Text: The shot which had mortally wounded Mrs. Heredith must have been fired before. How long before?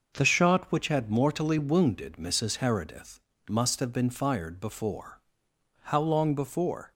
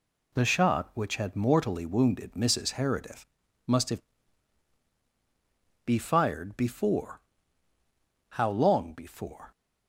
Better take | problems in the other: first | pauses between "Heredith" and "must"; at 3.2 s; 0.44 s long; slight in the first // says "be" for "been"; at 5.8 s

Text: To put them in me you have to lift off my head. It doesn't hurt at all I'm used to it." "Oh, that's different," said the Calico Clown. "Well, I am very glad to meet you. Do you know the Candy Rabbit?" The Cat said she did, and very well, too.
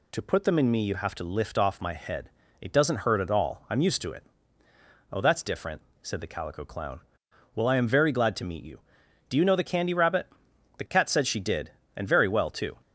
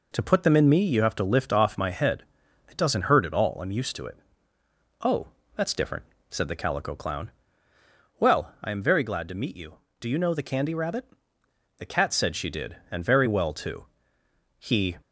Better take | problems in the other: first | goes on to say "He"; slight; from 14.5 s on; 0.38 s long

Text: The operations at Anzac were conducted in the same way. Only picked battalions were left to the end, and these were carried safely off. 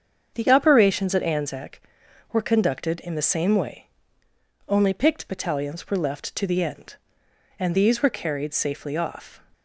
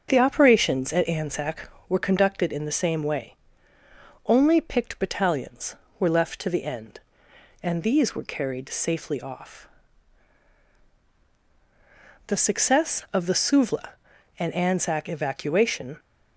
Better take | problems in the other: first | starts louder than the rest; strong; until 1.1 s; 7 dB; strong in the first // goes on to say "The success of the Suvla and Anzac evacuation"; strong; from 12.2 s on; 3.7 s long

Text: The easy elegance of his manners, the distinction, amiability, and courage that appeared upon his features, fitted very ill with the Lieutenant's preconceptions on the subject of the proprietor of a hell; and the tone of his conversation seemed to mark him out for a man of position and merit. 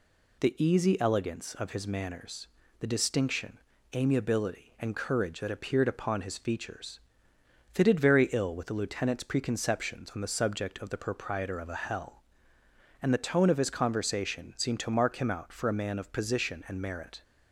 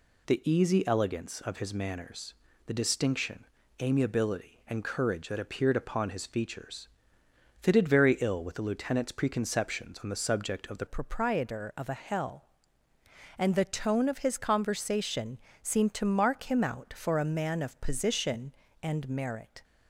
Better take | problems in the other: first | changes voice at "proprietor"; from 10.8 s on; 8.8 s long // pauses between "conversation" and "seemed"; slight; at 15.3 s; 0.24 s long

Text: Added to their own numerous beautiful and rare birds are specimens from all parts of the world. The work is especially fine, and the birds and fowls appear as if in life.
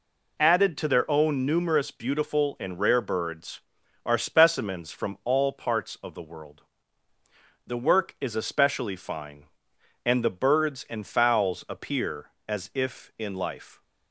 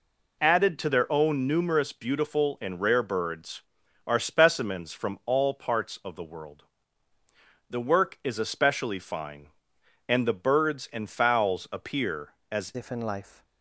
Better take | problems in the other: first | changes voice at "if"; from 12.7 s on; 0.7 s long

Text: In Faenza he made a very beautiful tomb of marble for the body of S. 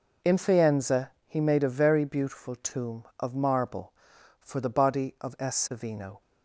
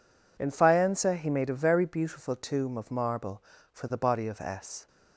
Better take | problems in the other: second | pauses between "Faenza" and "he"; slight; at 1.1 s; 0.16 s long // goes on to say "Savino"; from 5.7 s on; 0.50 s long

